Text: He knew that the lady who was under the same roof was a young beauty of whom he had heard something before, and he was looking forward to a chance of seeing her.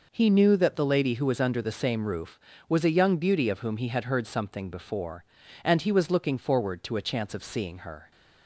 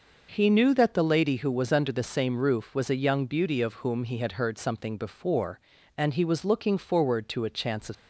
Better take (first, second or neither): first